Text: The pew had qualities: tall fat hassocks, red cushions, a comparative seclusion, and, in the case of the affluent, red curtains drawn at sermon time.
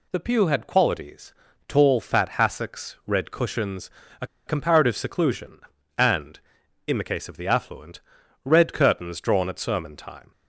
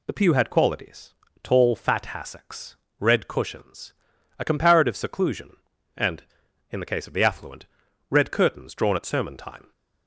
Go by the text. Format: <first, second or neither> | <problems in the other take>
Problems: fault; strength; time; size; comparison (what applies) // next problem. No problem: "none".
second | pauses between "a" and "comparative"; slight; at 4.2 s; 0.20 s long